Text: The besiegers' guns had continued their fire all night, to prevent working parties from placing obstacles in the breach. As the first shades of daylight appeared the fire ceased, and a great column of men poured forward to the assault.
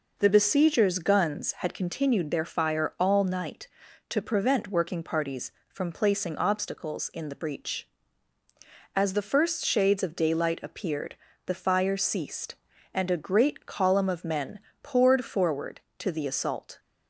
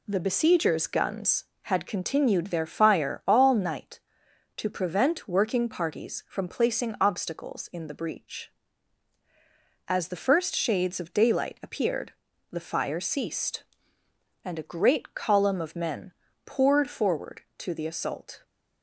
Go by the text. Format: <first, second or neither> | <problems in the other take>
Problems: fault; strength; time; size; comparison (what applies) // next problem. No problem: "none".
neither | pauses between "appeared" and "the"; the same in both // pauses between "men" and "poured"; slight; the same in both